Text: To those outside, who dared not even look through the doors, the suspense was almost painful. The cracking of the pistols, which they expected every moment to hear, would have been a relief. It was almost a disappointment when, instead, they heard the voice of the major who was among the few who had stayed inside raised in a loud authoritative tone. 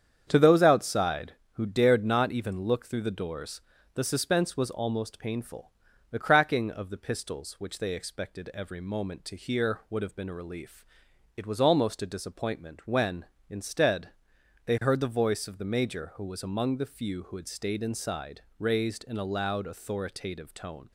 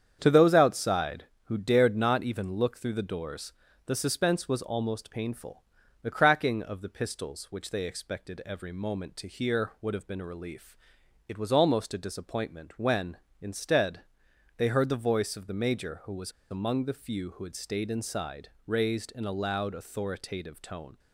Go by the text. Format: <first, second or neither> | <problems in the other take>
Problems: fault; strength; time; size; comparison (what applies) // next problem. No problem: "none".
first | starts louder than the rest; strong; until 1.2 s; 8 dB; strong in the first // pauses between "was" and "among"; slight; at 16.3 s; 0.21 s long // pauses between "inside" and "raised"; slight; at 18.4 s; 0.18 s long; slight in the first